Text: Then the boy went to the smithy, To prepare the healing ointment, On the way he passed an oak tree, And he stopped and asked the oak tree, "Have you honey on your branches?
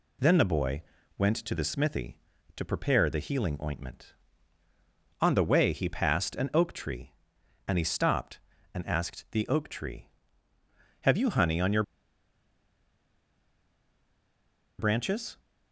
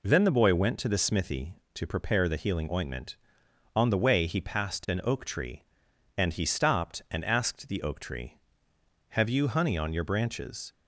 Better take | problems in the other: second | pauses between "boy" and "went"; slight; at 0.8 s; 0.34 s long // pauses between "your" and "branches"; strong; at 11.8 s; 2.9 s long

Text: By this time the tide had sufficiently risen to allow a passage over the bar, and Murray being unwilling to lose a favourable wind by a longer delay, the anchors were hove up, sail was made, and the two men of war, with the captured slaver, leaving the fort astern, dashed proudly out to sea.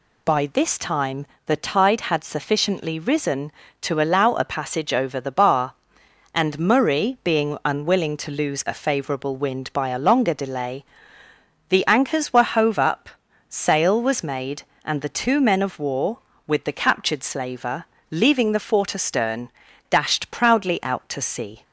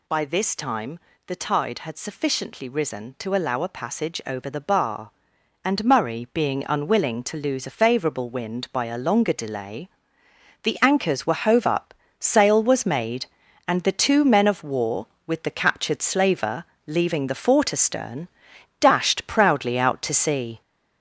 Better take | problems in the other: first | gets louder; noticeable; throughout; 5 dB // pauses between "time" and "the"; slight; at 0.9 s; 0.28 s long; slight in the first

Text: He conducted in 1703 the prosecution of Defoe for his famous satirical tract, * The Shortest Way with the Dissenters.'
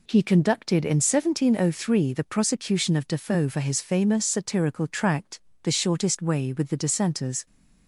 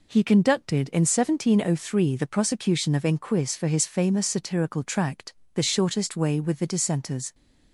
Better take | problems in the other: first | says "Inquis" for "Defoe"; at 3.0 s

